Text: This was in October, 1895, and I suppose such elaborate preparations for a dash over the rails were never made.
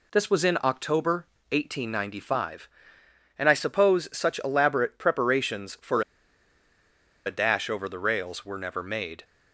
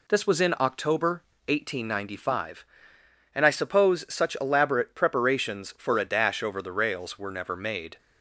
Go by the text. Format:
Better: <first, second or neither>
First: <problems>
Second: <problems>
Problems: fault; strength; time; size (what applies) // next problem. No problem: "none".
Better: second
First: pauses between "for" and "a"; at 6.0 s; 1.2 s long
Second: none